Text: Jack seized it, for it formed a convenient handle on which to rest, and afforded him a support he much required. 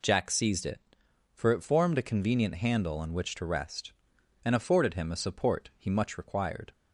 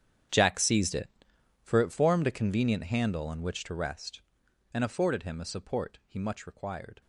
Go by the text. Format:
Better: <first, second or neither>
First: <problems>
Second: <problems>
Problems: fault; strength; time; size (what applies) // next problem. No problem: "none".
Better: first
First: none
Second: gets quieter; strong; throughout; 18 dB